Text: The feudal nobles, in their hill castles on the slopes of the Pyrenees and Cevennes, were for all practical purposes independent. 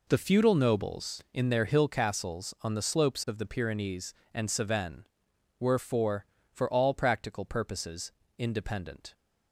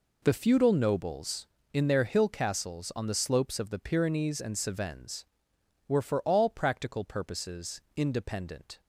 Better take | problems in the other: second | says "for" twice; at 6.5 s // pauses between "purposes" and "independent"; slight; at 8.1 s; 0.26 s long

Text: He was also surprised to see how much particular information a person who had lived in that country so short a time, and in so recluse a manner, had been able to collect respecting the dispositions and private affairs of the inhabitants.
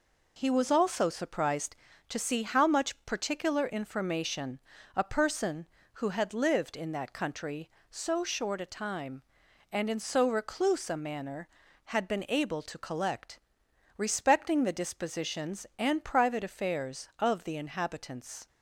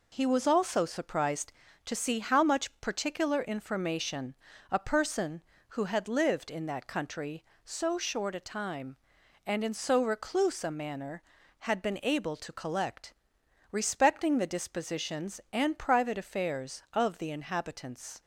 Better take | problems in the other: neither | pauses between "information" and "a"; slight; the same in both // pauses between "collect" and "respecting"; noticeable; the same in both

